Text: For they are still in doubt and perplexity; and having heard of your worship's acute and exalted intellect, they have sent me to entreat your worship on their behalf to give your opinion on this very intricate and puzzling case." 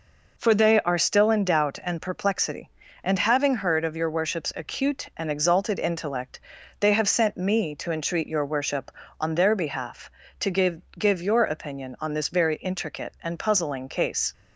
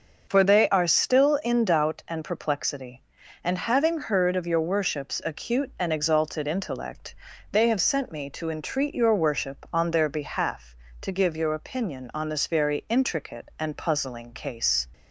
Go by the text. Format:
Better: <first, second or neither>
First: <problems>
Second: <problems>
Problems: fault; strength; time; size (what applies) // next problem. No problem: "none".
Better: second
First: says "give" twice; at 10.9 s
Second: none